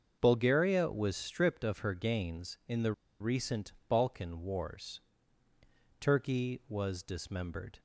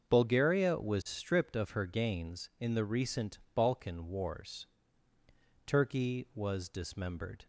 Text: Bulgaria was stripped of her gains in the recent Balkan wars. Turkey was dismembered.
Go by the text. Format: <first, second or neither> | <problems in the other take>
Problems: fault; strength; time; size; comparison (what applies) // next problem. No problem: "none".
second | starts louder than the rest; until 1.2 s; 6.5 dB; also in the second // pauses between "the" and "recent"; slight; at 2.9 s; 0.28 s long // pauses between "recent" and "Balkan"; slight; at 3.7 s; 0.16 s long; slight in the second